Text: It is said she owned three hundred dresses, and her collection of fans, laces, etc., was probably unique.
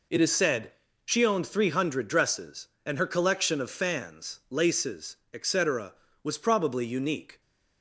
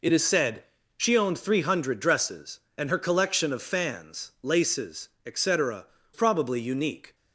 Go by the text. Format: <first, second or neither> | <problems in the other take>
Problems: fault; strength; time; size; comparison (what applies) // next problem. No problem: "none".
first | pauses between "said" and "she"; slight; at 0.6 s; 0.34 s long; slight in the first // skips "was"; at 5.9 s